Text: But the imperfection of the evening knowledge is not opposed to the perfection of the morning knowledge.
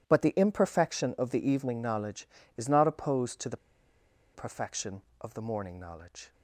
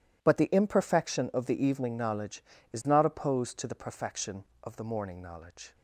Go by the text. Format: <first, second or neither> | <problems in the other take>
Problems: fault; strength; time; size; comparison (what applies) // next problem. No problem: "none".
second | pauses between "the" and "perfection"; noticeable; at 3.5 s; 0.77 s long